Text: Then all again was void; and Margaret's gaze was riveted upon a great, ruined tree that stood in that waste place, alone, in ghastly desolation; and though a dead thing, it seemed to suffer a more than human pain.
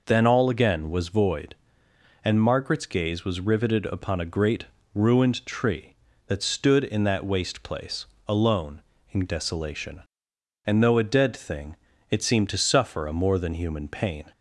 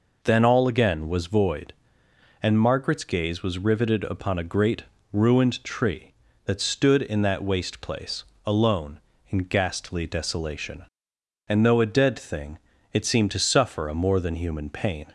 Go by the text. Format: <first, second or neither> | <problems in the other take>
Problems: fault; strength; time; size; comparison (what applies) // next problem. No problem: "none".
second | skips "ghastly"; at 9.2 s